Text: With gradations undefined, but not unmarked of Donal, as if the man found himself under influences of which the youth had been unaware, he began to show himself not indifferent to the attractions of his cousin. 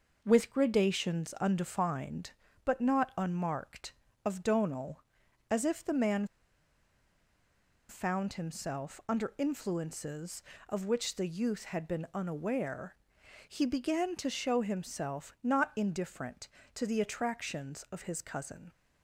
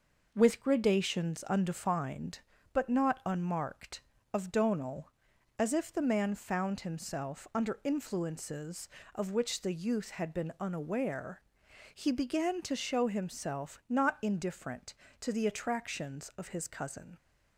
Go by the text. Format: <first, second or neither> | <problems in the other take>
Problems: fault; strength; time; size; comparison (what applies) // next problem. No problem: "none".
second | pauses between "man" and "found"; strong; at 6.2 s; 1.6 s long